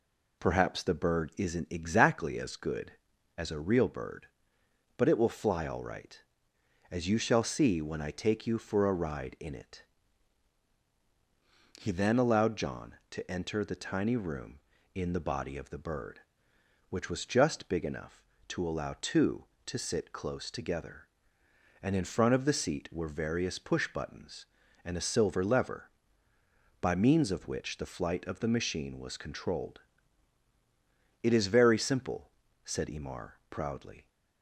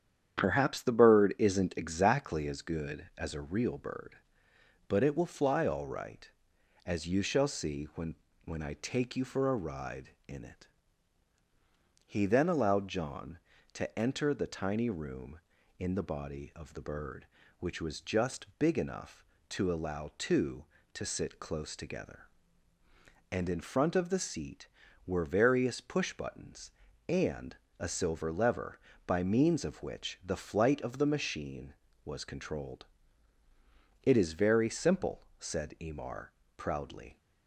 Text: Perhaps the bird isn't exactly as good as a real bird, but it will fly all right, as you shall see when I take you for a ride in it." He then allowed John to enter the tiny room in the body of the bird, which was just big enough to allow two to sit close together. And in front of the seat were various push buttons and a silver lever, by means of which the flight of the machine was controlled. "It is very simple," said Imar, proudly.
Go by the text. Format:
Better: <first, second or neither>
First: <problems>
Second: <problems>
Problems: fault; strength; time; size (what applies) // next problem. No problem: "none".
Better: first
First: none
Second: starts louder than the rest; strong; until 1.4 s; 9 dB // says "when" twice; at 8.4 s // pauses between "and" and "a"; slight; at 27.5 s; 0.24 s long